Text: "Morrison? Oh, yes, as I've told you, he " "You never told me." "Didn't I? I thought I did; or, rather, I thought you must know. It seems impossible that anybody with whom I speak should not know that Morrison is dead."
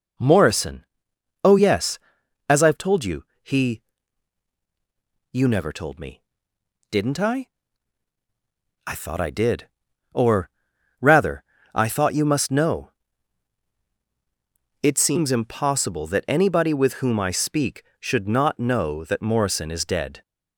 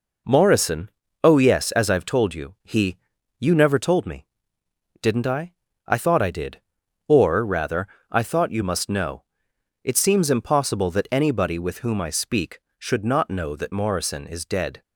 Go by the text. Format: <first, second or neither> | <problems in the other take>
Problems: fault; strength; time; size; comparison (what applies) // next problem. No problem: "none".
second | gets louder; strong; throughout; 9.5 dB